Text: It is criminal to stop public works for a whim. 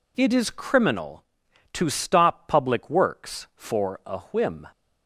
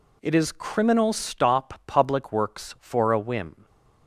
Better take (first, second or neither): first